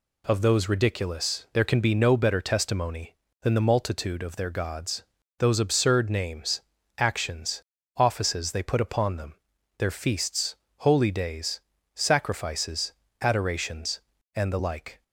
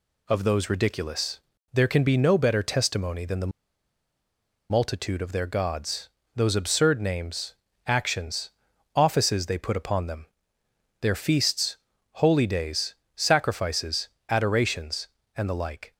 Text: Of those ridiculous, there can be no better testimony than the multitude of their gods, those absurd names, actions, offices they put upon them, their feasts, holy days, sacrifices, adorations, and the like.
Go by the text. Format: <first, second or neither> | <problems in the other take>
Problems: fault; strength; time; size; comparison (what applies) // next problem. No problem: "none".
first | pauses between "the" and "multitude"; at 3.5 s; 1.1 s long